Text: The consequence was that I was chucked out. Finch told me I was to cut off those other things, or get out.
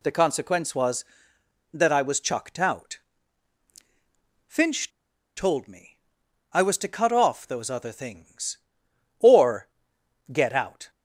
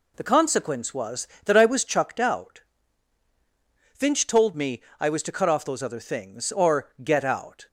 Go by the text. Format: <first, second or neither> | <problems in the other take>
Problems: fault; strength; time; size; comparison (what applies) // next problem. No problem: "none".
second | pauses between "Finch" and "told"; noticeable; at 4.8 s; 0.48 s long // pauses between "me" and "I"; noticeable; at 5.9 s; 0.54 s long; slight in the second // pauses between "or" and "get"; noticeable; at 9.6 s; 0.64 s long